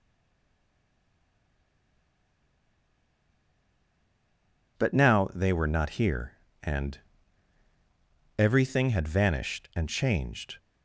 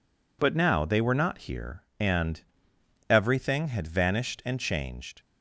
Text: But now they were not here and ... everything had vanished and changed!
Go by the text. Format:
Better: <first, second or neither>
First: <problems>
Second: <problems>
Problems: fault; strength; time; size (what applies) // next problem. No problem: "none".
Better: second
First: stays silent before the first word; strong; until 4.7 s; 4.7 s long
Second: none